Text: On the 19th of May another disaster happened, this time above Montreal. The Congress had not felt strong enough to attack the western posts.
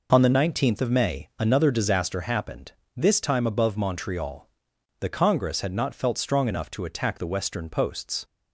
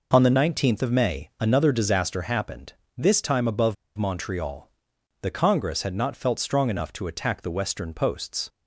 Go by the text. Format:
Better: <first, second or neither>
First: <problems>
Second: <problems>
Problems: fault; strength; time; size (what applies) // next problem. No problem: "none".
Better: first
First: none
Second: pauses between "above" and "Montreal"; slight; at 3.7 s; 0.23 s long